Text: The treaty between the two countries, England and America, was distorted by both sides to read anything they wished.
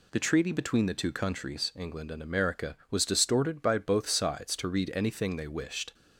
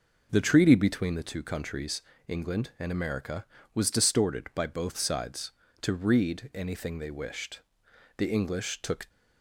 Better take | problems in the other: first | goes on to say "The English took"; noticeable; from 8.1 s on; 0.92 s long

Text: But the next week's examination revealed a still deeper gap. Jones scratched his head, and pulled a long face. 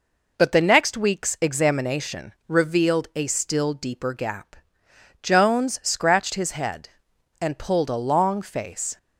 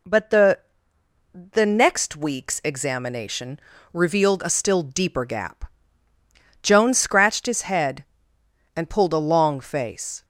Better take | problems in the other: first | says "the" twice; at 1.3 s // pauses between "examination" and "revealed"; slight; at 3.6 s; 0.32 s long; slight in the first

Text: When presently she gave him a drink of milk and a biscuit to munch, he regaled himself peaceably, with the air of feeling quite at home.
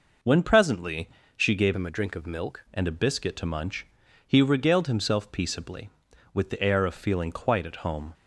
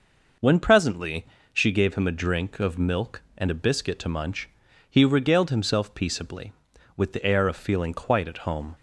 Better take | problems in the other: second | pauses between "presently" and "she"; slight; at 1.0 s; 0.28 s long; slight in the second // changes voice from "him" to "milk"; from 1.7 to 2.6 s; 0.9 s long

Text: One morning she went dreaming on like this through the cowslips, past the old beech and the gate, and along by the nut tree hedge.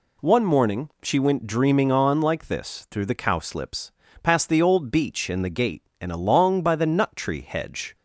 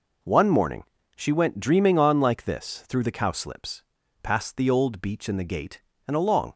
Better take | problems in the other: first | pauses between "morning" and "she"; slight; at 0.8 s; 0.32 s long // stops before "by the nut tree hedge"; at 6.5 s

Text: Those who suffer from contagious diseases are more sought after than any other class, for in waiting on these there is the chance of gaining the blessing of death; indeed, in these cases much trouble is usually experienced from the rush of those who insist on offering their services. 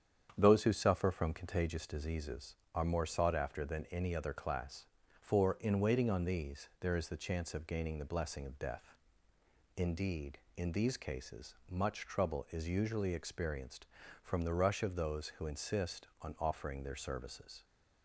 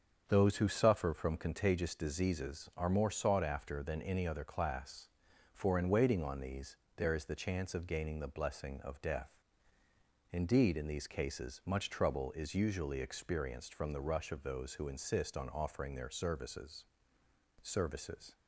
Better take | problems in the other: first | starts louder than the rest; strong; until 1.2 s; 7 dB; strong in the first // pauses between "these" and "there"; slight; at 6.7 s; 0.18 s long // says "services" twice; at 17.6 s

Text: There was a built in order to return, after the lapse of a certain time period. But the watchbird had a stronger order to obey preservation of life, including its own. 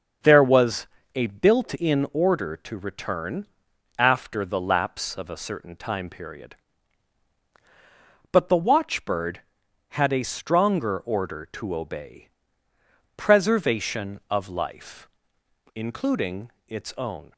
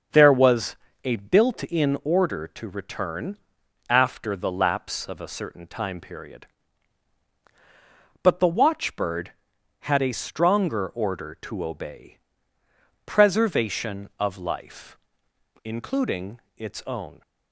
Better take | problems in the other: neither | starts louder than the rest; the same in both // pauses between "was" and "a"; slight; the same in both // pauses between "obey" and "preservation"; noticeable; the same in both // pauses between "including" and "its"; slight; the same in both

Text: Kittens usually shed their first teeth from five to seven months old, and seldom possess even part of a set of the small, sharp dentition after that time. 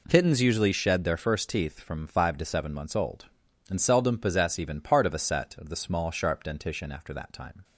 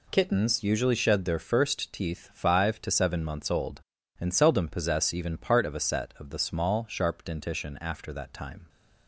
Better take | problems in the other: first | skips "from"; at 2.3 s

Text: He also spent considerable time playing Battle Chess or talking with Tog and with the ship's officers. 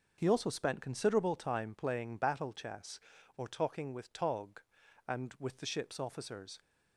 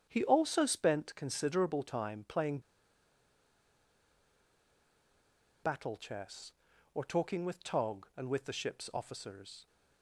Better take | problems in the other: first | starts louder than the rest; strong; until 1.1 s; 8.5 dB // pauses between "playing" and "Battle"; strong; at 2.5 s; 3.0 s long

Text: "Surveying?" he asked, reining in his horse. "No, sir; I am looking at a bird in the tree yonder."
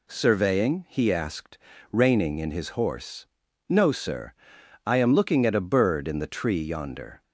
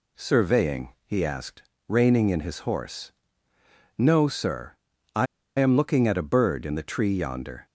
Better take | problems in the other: first | pauses between "I" and "am"; slight; at 5.2 s; 0.31 s long

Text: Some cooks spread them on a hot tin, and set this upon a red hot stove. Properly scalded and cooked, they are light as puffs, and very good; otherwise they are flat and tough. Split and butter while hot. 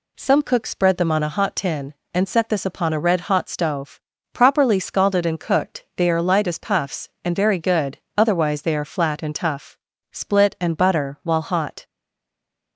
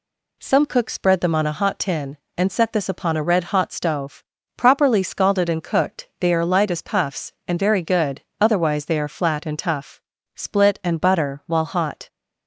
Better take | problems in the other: second | stays silent after the last word; slight; from 11.8 s on; 0.9 s long

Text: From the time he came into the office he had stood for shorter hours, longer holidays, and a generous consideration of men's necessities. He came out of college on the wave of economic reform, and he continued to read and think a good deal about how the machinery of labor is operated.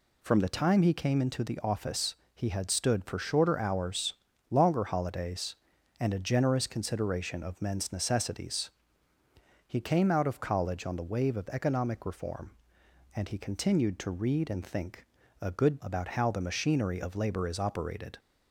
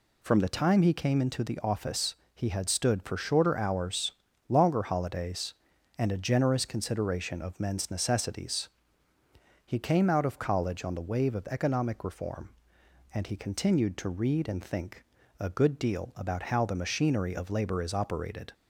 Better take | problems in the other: second | pauses between "office" and "he"; slight; at 2.1 s; 0.18 s long; slight in the second // pauses between "think" and "a"; slight; at 15.0 s; 0.36 s long; slight in the second // skips "deal"; at 15.8 s

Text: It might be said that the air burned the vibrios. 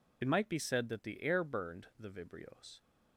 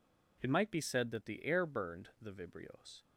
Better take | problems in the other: second | loses the start of "It"; at 0.2 s; 35 ms

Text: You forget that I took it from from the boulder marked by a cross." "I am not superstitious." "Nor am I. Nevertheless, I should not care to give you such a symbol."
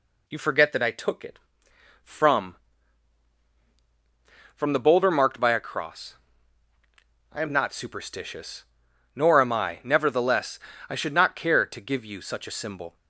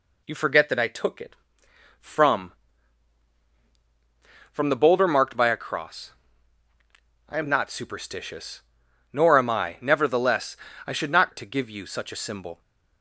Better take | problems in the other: first | skips "care"; at 11.3 s

